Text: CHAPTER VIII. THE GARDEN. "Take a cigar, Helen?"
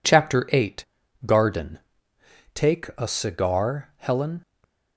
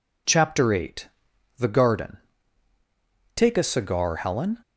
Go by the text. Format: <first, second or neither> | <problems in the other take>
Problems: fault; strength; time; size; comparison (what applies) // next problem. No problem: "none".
second | skips "THE"; at 1.0 s // stays silent after the last word; slight; from 4.4 s on; 0.5 s long